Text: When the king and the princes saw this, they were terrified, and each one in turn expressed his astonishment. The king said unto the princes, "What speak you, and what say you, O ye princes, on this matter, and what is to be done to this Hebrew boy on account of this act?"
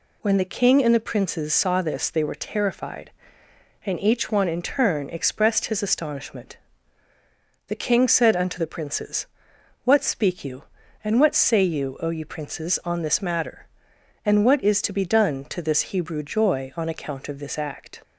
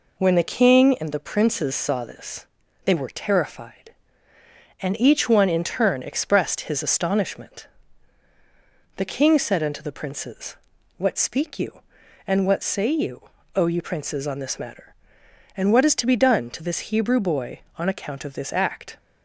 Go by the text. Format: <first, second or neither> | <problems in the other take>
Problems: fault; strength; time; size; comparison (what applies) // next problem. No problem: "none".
second | says "joy" for "boy"; at 16.2 s